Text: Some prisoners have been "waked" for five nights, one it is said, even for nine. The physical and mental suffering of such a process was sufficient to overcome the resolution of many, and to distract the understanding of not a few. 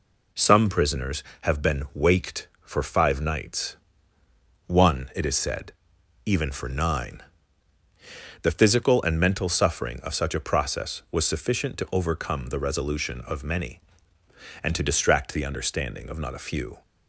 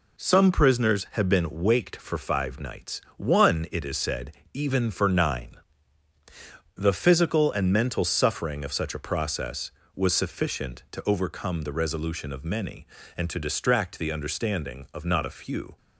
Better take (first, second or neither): neither